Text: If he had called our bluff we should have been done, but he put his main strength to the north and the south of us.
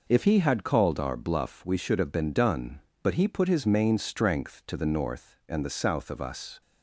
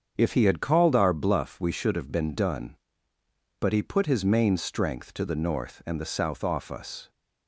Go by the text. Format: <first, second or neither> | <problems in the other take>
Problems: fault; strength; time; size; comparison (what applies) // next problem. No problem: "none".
first | starts louder than the rest; strong; until 1.1 s; 7.5 dB // says "off" for "of"; at 6.4 s